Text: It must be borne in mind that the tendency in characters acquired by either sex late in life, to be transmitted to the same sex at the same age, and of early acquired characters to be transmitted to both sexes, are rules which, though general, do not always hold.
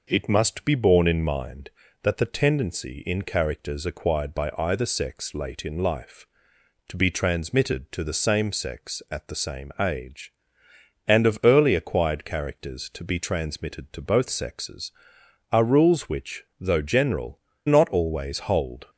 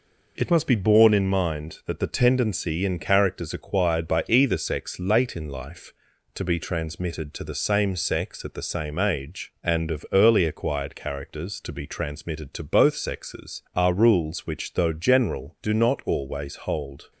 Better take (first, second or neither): second